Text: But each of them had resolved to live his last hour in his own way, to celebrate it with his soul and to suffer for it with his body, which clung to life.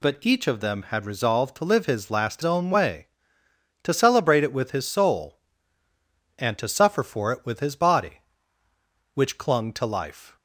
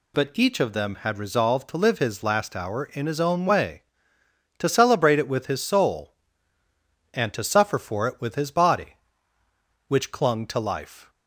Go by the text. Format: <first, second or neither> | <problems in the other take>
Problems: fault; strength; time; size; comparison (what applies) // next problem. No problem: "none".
second | skips "hour in his"; at 2.4 s